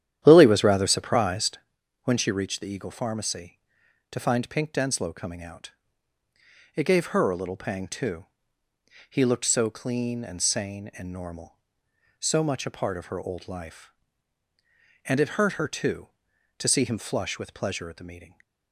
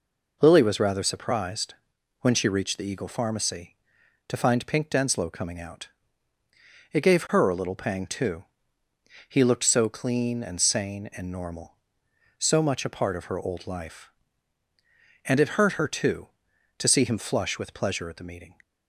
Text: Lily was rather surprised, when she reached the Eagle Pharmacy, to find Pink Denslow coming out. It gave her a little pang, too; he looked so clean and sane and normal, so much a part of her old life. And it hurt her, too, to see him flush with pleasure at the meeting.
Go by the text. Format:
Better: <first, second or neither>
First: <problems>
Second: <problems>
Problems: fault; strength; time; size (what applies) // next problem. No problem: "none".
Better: second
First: starts louder than the rest; strong; until 1.6 s; 10.5 dB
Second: none